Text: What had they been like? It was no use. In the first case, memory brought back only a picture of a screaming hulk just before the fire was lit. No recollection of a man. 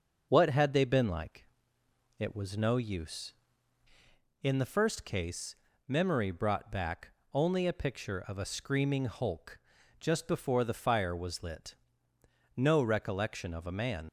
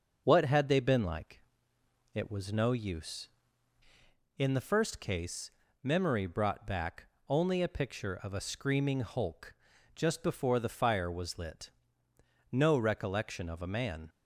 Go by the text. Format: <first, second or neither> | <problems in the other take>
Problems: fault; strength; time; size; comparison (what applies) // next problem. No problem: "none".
second | starts louder than the rest; noticeable; until 1.3 s; 6 dB; noticeable in the second // pauses between "back" and "only"; slight; at 7.0 s; 0.24 s long; slight in the second // pauses between "hulk" and "just"; at 9.5 s; 0.42 s long; also in the second // leaves "man" unfinished; at 14.0 s; 45 ms